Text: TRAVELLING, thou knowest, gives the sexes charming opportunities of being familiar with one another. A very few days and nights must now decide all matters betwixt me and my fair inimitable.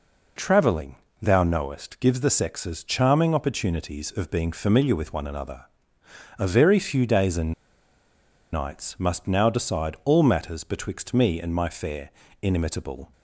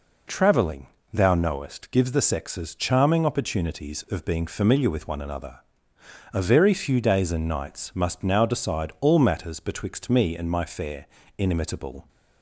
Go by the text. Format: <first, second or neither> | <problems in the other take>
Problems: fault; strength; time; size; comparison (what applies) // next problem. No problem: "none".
second | pauses between "and" and "nights"; at 7.5 s; 0.99 s long // pauses between "fair" and "inimitable"; slight; at 12.0 s; 0.32 s long; slight in the second